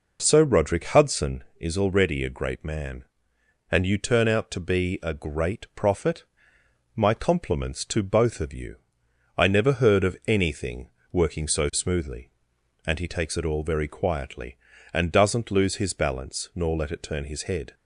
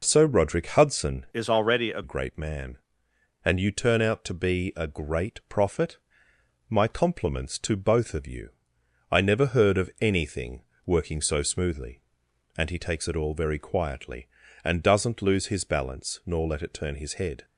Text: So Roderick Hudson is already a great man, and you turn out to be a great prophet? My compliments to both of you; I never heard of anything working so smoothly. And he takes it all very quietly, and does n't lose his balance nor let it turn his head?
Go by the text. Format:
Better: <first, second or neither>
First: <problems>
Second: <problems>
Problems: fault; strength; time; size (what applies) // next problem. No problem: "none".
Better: first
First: pauses between "anything" and "working"; slight; at 10.8 s; 0.22 s long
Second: changes voice from "is" to "a"; from 1.3 to 2.0 s; 0.7 s long // pauses between "anything" and "working"; slight; at 10.6 s; 0.22 s long